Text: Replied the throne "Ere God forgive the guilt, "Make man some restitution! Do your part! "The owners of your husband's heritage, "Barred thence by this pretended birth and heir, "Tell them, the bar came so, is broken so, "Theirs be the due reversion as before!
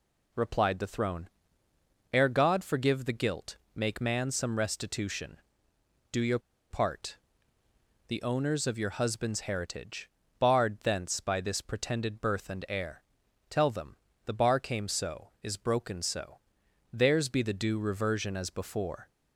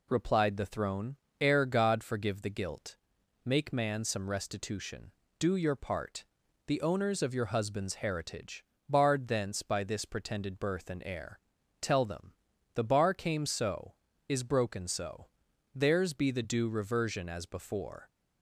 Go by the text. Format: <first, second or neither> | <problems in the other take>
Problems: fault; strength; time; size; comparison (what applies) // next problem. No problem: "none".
second | pauses between "throne" and "Ere"; noticeable; at 1.2 s; 0.82 s long; slight in the second // pauses between "your" and "part"; slight; at 6.3 s; 0.32 s long